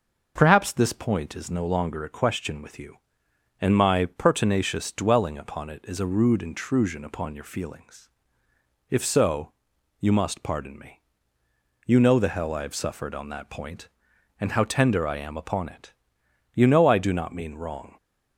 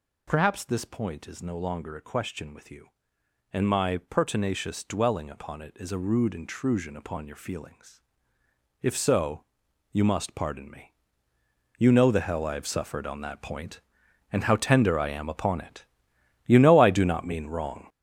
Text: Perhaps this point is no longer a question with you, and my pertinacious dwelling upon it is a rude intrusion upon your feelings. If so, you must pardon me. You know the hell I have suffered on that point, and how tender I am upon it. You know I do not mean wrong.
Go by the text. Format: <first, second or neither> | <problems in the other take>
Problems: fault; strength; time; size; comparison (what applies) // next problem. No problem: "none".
first | gets louder; strong; throughout; 7.5 dB